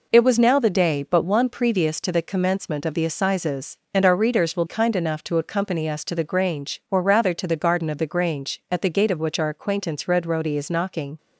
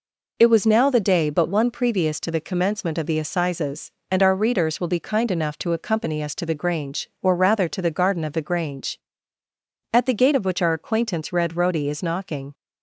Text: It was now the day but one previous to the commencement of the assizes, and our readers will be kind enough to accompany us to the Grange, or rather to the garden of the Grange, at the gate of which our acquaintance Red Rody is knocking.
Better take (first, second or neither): second